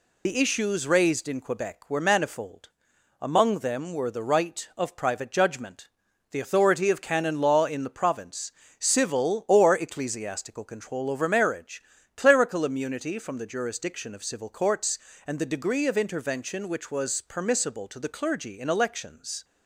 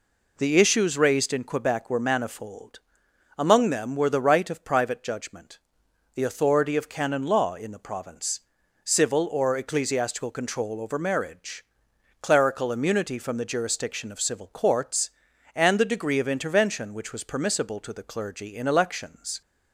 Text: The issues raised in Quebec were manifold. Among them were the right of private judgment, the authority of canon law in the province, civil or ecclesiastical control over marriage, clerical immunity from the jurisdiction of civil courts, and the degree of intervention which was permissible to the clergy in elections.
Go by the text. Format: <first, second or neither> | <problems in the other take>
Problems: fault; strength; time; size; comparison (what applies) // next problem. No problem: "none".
second | loses the start of "The"; at 0.2 s; 70 ms